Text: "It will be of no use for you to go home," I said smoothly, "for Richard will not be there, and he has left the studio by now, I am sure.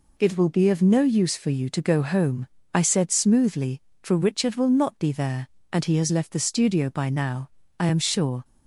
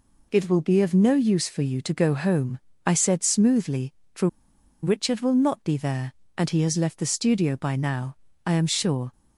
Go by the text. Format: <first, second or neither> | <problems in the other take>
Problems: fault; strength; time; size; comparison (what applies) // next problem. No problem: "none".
first | pauses between "for" and "Richard"; noticeable; at 4.2 s; 0.56 s long